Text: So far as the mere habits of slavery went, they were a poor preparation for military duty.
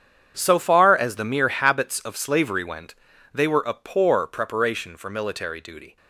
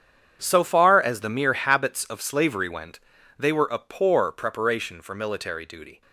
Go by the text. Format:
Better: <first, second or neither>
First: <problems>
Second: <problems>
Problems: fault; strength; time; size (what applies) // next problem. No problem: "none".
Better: neither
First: starts louder than the rest; strong; until 1.3 s; 8.5 dB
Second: starts louder than the rest; strong; until 1.4 s; 8.5 dB